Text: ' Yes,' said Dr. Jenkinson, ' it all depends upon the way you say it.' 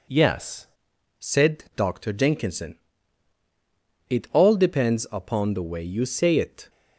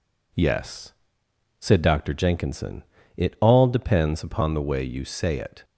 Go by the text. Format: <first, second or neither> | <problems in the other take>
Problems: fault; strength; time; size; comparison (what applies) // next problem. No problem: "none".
second | changes voice at "said"; from 1.1 s on; 5.5 s long